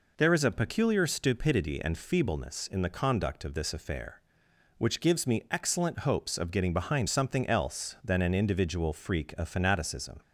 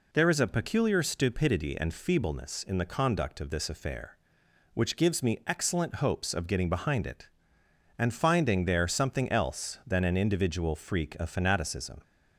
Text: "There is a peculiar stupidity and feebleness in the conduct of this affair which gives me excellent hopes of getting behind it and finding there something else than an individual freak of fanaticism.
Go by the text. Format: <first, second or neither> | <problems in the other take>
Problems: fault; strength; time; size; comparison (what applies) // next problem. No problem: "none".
second | skips "it and finding there"; at 7.0 s